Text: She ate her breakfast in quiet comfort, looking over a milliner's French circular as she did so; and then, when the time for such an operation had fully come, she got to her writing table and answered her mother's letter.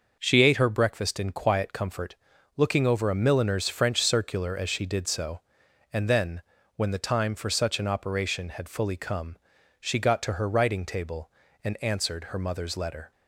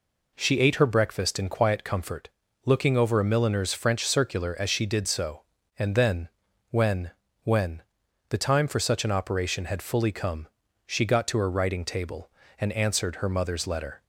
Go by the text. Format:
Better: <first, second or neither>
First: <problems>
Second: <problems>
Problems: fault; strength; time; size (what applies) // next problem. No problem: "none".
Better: first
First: none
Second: says "when" twice; at 7.4 s